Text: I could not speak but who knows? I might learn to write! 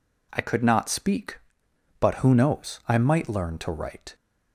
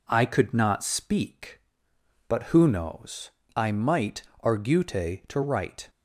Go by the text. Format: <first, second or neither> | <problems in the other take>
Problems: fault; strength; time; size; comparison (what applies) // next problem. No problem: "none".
first | says "argute" for "learn"; at 4.4 s